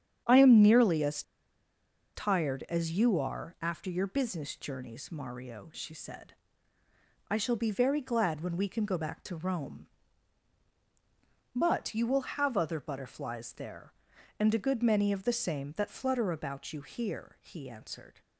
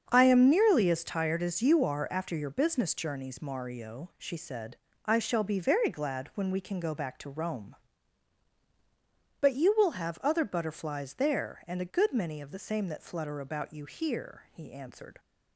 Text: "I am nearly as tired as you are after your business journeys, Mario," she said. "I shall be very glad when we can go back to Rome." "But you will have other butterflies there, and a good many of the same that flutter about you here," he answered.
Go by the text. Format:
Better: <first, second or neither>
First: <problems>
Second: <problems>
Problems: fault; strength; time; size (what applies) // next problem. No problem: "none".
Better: second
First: starts louder than the rest; strong; until 2.2 s; 8.5 dB // pauses between "as" and "tired"; noticeable; at 1.2 s; 0.93 s long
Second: starts louder than the rest; strong; until 1.1 s; 7 dB